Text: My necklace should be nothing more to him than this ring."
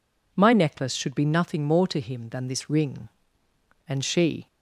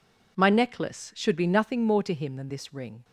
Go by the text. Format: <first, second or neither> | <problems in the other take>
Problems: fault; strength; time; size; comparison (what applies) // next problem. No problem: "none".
second | goes on to say "And she"; from 3.8 s on; 0.58 s long